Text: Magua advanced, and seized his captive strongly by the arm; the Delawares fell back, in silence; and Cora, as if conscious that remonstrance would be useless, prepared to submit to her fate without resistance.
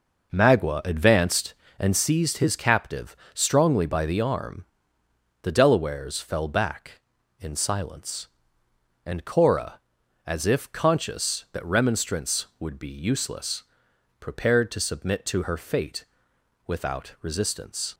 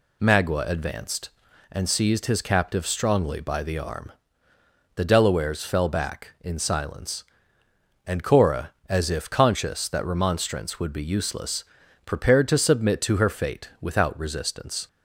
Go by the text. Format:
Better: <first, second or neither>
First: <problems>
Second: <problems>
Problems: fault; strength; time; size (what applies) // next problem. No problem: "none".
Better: second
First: starts louder than the rest; noticeable; until 2.1 s; 5.5 dB // pauses between "captive" and "strongly"; slight; at 3.1 s; 0.18 s long // pauses between "fate" and "without"; noticeable; at 16.0 s; 0.62 s long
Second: none